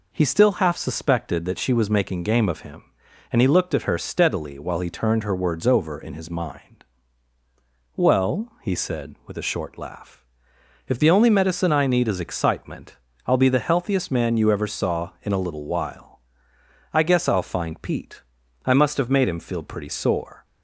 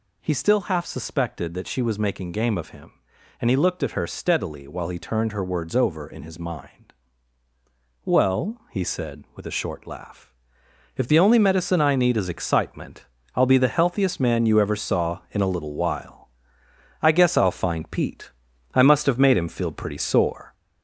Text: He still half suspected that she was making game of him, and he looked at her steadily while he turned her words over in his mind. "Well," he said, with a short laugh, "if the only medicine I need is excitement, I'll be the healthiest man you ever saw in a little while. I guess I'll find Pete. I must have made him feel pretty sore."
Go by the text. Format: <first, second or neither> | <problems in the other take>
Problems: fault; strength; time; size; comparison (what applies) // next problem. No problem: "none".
first | gets louder; throughout; 4 dB